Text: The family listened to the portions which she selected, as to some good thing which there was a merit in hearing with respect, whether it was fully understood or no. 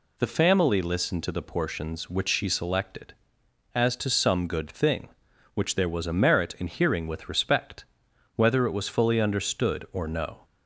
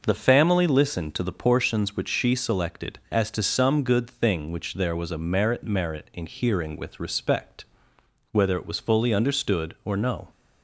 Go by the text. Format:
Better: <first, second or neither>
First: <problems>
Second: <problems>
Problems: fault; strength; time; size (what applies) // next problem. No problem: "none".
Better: first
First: none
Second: says "merit" twice; at 5.6 s